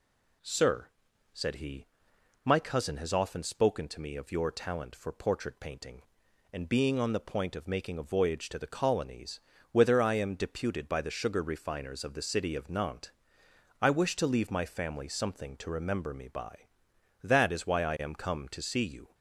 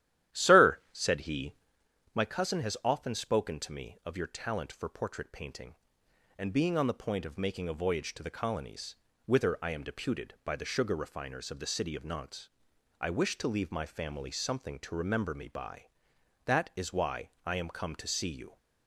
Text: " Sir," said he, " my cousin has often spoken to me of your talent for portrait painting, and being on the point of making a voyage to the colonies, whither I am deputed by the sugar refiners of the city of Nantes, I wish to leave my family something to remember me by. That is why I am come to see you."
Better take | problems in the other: first | starts louder than the rest; strong; until 1.9 s; 12.5 dB // pauses between "why" and "I"; slight; at 17.3 s; 0.16 s long

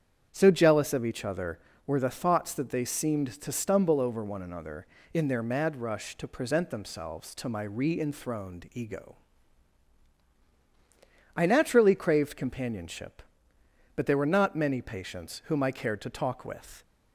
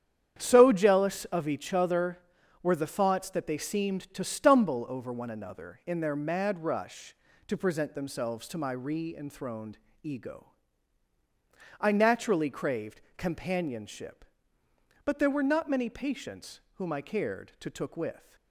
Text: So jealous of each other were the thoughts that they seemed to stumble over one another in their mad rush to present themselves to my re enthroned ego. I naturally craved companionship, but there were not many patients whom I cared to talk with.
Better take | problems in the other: first | starts louder than the rest; strong; until 1.4 s; 9 dB; strong in the first // pauses between "enthroned" and "ego"; slight; at 9.7 s; 0.26 s long // pauses between "craved" and "companionship"; slight; at 13.0 s; 0.16 s long // pauses between "patients" and "whom"; slight; at 16.5 s; 0.16 s long // says "took" for "talk"; at 17.6 s

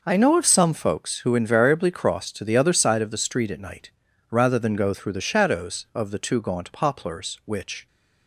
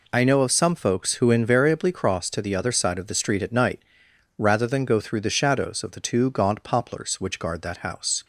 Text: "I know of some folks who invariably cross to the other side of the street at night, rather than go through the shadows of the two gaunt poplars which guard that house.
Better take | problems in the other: second | stops before "guard that house"; at 7.8 s

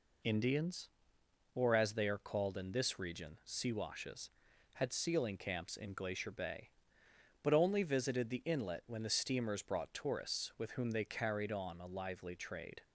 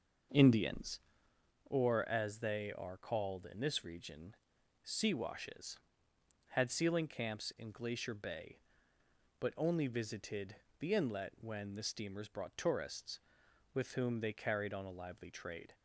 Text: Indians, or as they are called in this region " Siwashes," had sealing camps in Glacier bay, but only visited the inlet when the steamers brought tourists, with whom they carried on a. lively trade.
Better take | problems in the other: first | starts louder than the rest; noticeable; until 1.5 s; 6 dB // pauses between "visited" and "the"; slight; at 10.5 s; 0.24 s long

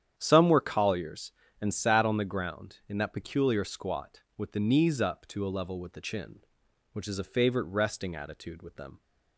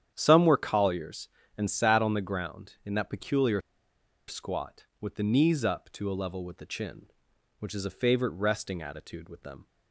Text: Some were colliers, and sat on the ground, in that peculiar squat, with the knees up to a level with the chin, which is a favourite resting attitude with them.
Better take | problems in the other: first | starts louder than the rest; strong; until 1.1 s; 9.5 dB; strong in the first // pauses between "peculiar" and "squat"; noticeable; at 3.5 s; 0.68 s long

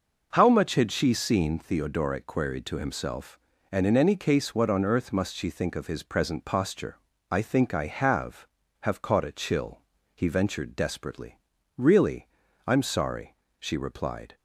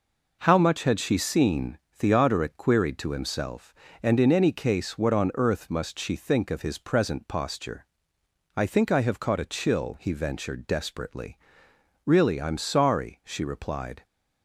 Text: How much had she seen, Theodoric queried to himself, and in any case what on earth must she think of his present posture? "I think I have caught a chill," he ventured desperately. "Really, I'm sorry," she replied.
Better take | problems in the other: second | says "have" twice; at 8.8 s

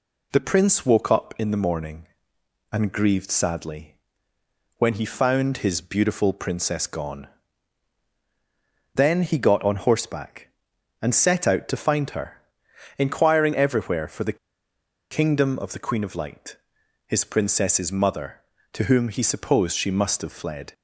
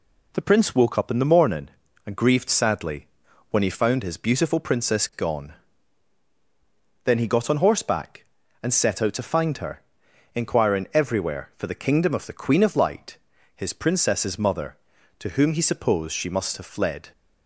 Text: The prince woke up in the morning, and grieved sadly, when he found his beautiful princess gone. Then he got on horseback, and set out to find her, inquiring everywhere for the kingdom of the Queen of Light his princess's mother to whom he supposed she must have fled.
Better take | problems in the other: second | pauses between "the" and "kingdom"; noticeable; at 14.3 s; 0.74 s long // pauses between "Light" and "his"; noticeable; at 16.5 s; 0.50 s long; also in the second

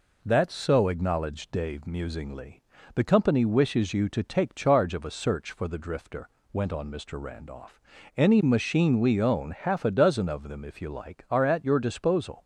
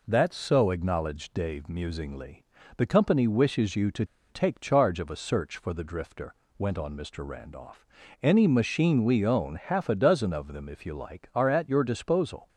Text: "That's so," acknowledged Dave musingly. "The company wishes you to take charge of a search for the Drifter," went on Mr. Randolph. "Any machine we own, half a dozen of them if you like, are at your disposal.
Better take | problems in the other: first | pauses between "to" and "take"; slight; at 4.0 s; 0.25 s long

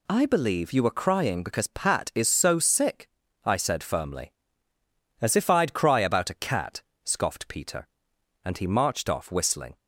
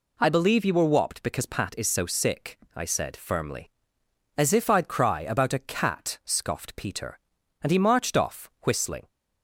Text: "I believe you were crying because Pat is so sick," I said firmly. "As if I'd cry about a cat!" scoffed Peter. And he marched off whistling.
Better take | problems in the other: first | says "whopped" for "crying"; at 0.9 s

